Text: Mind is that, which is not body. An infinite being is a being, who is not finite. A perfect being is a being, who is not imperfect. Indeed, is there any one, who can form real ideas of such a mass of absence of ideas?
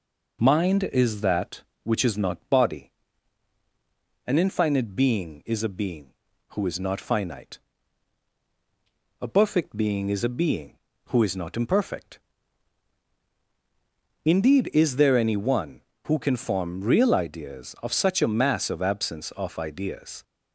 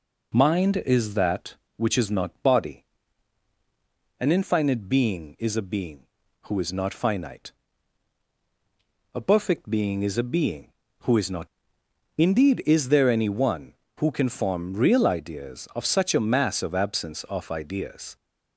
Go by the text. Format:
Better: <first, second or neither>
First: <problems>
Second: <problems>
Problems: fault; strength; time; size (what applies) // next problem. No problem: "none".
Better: first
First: none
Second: skips "imperfect"; at 11.8 s